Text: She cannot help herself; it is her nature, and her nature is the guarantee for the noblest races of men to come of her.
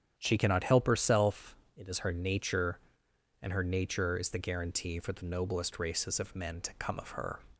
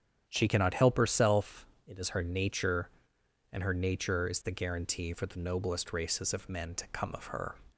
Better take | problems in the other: neither | starts louder than the rest; strong; the same in both

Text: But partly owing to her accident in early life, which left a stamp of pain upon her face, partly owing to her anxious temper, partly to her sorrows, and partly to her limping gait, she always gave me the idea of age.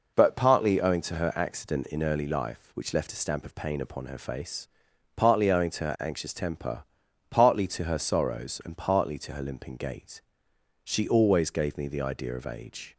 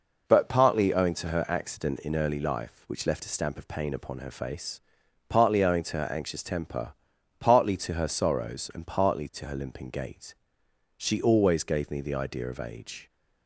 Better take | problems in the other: neither | none

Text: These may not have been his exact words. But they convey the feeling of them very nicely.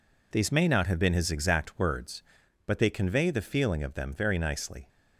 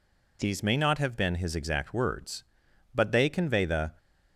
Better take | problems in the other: first | stops before "feeling of them very nicely"; at 3.9 s

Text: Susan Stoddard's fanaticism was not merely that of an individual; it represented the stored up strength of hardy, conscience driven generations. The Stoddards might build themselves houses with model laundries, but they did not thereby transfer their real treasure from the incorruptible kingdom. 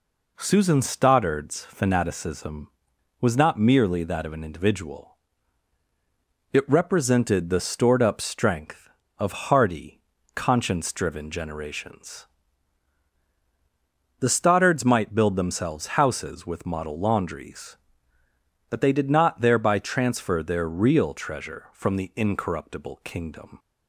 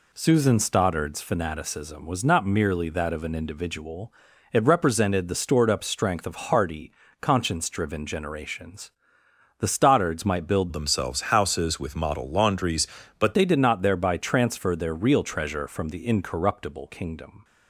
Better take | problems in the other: first | changes voice from "themselves" to "but"; from 10.7 to 13.3 s; 2.6 s long

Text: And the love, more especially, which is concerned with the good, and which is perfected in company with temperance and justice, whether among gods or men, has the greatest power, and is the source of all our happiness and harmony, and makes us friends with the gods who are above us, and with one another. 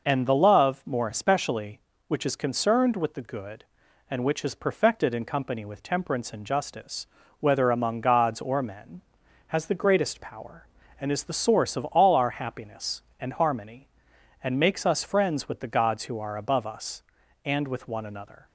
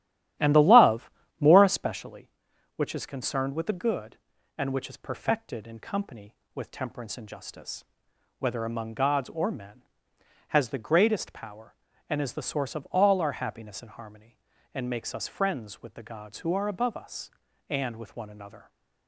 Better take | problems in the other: first | starts louder than the rest; strong; until 2.1 s; 13 dB

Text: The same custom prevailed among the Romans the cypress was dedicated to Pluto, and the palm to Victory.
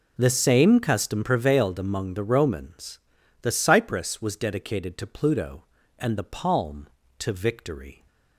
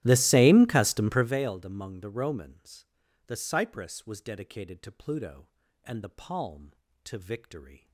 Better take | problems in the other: first | starts louder than the rest; strong; until 1.4 s; 14 dB // pauses between "Romans" and "the"; at 2.8 s; 0.42 s long; also in the first

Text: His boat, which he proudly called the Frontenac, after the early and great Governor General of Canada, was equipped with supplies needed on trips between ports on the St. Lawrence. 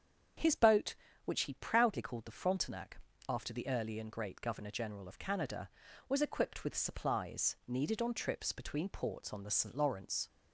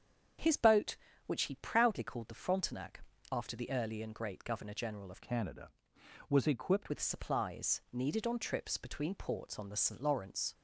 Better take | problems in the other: first | starts louder than the rest; strong; until 1.7 s; 7.5 dB; strong in the first // changes voice from "Canada" to "equipped"; from 5.2 to 6.9 s; 1.7 s long

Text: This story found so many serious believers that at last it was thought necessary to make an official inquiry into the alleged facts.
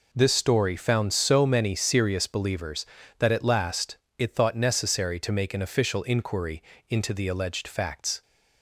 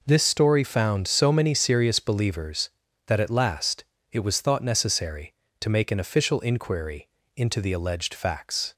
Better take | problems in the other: second | pauses between "last" and "it"; slight; at 3.9 s; 0.22 s long; slight in the second // skips "was"; at 4.3 s // pauses between "inquiry" and "into"; slight; at 6.6 s; 0.28 s long; slight in the second

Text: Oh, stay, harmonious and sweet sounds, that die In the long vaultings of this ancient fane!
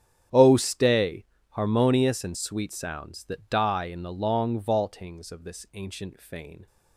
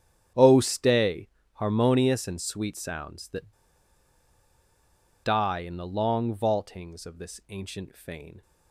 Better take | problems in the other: first | starts louder than the rest; strong; until 1.6 s; 9.5 dB; strong in the first // pauses between "that" and "die"; strong; at 3.5 s; 1.7 s long

